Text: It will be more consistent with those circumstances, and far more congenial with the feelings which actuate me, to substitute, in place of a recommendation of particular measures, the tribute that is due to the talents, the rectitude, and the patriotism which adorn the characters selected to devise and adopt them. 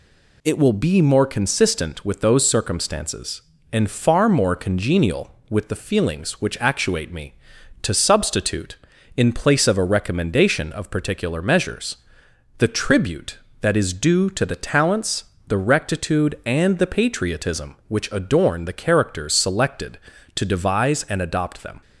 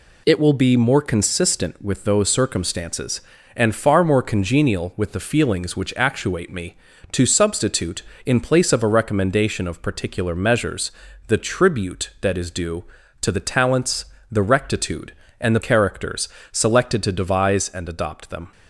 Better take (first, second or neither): first